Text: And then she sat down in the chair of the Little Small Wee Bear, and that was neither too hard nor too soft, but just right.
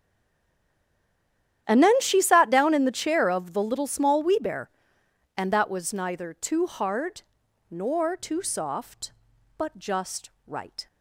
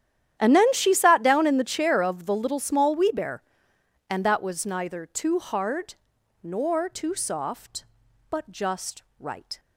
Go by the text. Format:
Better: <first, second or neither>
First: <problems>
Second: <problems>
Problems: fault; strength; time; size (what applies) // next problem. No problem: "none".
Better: second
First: stays silent before the first word; noticeable; until 1.6 s; 1.6 s long // starts louder than the rest; strong; until 2.6 s; 10.5 dB // pauses between "hard" and "nor"; noticeable; at 7.2 s; 0.48 s long // pauses between "just" and "right"; slight; at 10.2 s; 0.18 s long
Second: starts louder than the rest; strong; until 1.4 s; 10.5 dB // pauses between "hard" and "nor"; noticeable; at 5.9 s; 0.48 s long // pauses between "just" and "right"; slight; at 9.0 s; 0.18 s long